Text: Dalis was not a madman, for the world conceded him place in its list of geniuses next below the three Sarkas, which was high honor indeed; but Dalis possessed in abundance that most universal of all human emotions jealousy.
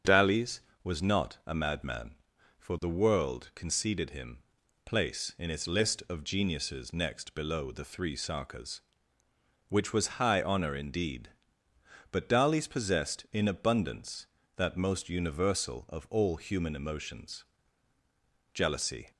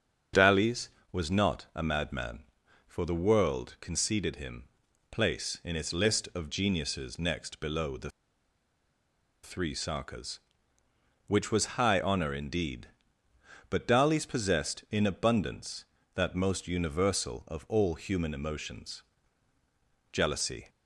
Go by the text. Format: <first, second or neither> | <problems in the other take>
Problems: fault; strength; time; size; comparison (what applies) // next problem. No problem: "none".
first | starts louder than the rest; until 1.5 s; 7 dB; also in the first // pauses between "him" and "place"; noticeable; at 4.6 s; 0.48 s long; noticeable in the first // pauses between "the" and "three"; strong; at 8.1 s; 1.3 s long // pauses between "emotions" and "jealousy"; at 19.0 s; 1.1 s long; also in the first